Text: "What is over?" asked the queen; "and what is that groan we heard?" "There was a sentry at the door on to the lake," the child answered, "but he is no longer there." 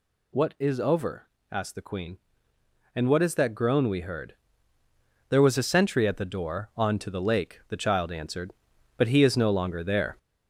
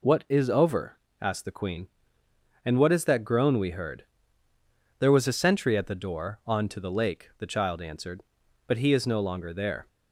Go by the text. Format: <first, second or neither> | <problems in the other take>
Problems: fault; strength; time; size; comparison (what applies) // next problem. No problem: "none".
second | gets louder; noticeable; throughout; 4.5 dB